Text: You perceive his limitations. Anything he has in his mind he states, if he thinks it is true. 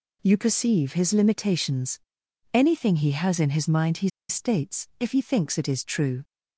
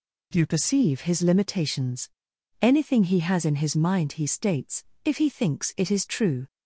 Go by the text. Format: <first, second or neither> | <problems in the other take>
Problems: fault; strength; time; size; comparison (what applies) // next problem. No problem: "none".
second | pauses between "he" and "states"; slight; at 4.0 s; 0.20 s long